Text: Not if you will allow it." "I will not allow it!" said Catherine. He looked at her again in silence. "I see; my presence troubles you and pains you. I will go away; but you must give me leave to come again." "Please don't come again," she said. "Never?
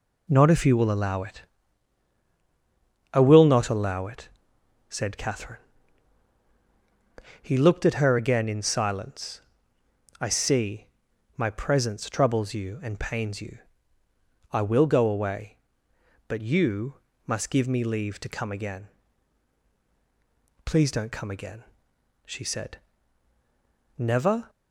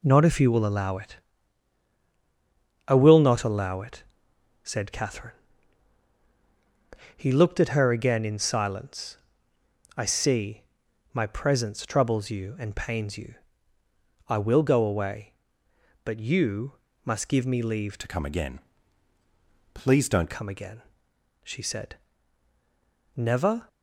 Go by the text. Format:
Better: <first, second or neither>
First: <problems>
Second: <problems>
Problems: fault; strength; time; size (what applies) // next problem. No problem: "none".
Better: first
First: pauses between "you" and "must"; slight; at 16.9 s; 0.32 s long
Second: pauses between "you" and "must"; slight; at 16.7 s; 0.32 s long // changes voice from "to" to "don't"; from 17.9 to 20.3 s; 2.4 s long